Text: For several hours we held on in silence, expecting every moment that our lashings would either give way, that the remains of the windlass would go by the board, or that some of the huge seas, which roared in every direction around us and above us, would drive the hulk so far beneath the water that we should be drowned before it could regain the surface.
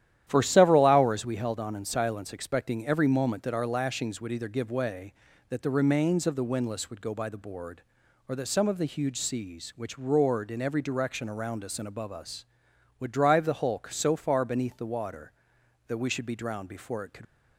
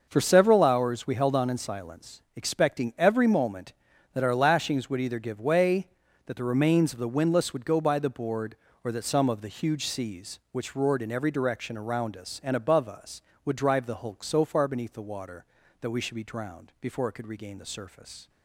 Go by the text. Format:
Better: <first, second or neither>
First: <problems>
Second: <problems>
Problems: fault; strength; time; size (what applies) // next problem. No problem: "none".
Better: second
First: starts louder than the rest; strong; until 1.2 s; 11.5 dB // stops before "regain the surface"; at 17.2 s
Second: none